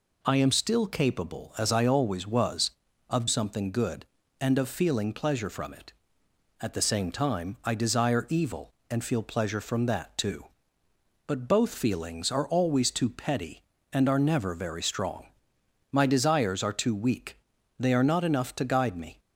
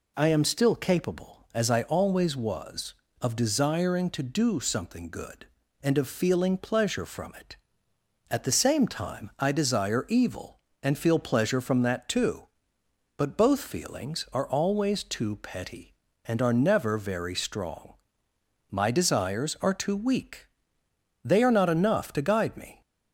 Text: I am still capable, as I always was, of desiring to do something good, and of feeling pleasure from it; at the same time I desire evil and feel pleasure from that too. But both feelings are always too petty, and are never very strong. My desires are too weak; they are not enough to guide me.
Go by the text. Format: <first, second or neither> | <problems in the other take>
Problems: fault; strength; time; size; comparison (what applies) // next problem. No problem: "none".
second | skips "desiring to do"; at 3.2 s